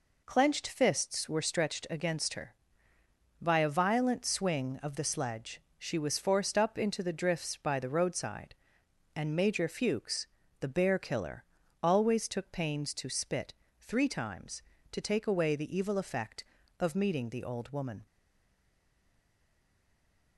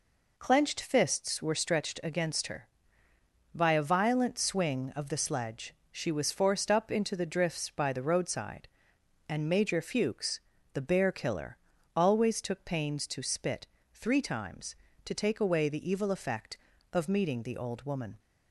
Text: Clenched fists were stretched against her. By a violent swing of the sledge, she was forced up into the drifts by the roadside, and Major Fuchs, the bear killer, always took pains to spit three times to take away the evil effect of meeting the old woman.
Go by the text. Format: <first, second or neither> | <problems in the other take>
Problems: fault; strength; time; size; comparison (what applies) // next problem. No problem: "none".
second | pauses between "spit" and "three"; slight; at 13.5 s; 0.26 s long; slight in the second // stays silent after the last word; from 18.0 s on; 2.3 s long